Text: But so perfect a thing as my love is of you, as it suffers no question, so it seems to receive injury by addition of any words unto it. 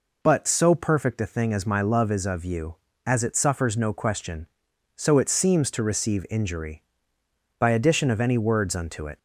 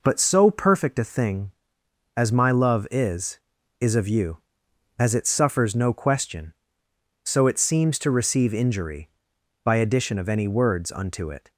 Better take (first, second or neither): first